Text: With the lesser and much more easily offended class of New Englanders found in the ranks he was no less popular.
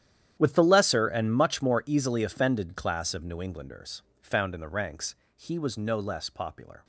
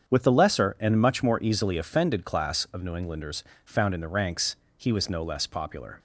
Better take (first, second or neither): second